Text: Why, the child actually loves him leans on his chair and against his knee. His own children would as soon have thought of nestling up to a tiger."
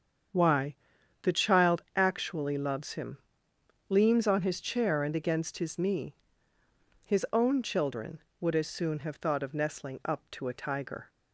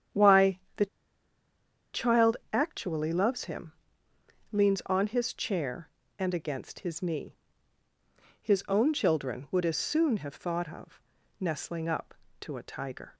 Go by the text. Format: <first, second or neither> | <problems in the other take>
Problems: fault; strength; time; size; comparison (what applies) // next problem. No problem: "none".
first | starts louder than the rest; strong; until 2.3 s; 9 dB; strong in the first // pauses between "the" and "child"; at 0.8 s; 1.0 s long // pauses between "child" and "actually"; slight; at 2.3 s; 0.18 s long // pauses between "him" and "leans"; noticeable; at 3.7 s; 0.80 s long; noticeable in the first // pauses between "of" and "nestling"; at 11.0 s; 0.38 s long